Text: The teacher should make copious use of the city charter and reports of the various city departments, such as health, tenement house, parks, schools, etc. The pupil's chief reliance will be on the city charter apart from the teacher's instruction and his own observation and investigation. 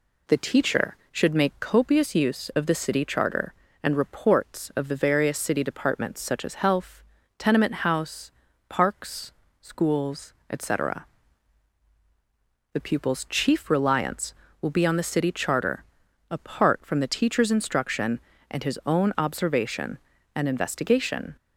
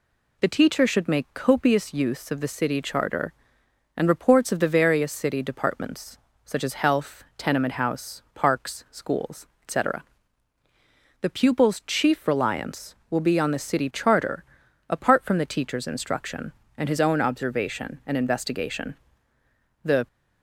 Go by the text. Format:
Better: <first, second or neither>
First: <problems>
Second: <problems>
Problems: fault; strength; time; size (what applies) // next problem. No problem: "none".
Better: first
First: pauses between "charter" and "apart"; noticeable; at 15.8 s; 0.48 s long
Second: pauses between "charter" and "apart"; at 14.4 s; 0.44 s long // goes on to say "The"; slight; from 19.8 s on; 0.24 s long